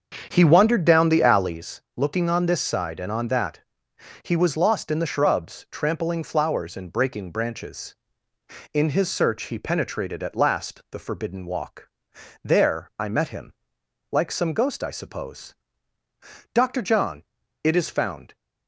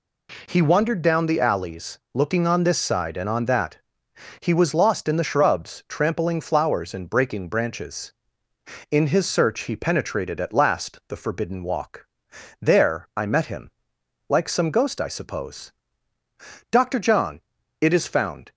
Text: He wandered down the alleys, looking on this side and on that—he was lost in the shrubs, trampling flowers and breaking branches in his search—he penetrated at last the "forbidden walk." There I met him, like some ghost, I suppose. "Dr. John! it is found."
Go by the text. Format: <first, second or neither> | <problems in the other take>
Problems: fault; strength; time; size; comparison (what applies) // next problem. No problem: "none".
second | starts louder than the rest; strong; until 1.7 s; 7 dB